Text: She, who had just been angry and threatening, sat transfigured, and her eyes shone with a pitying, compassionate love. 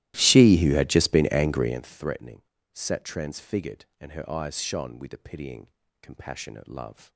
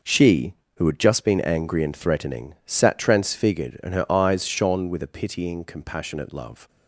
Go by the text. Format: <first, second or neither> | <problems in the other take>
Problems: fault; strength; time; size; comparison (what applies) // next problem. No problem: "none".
second | starts louder than the rest; strong; until 1.8 s; 15 dB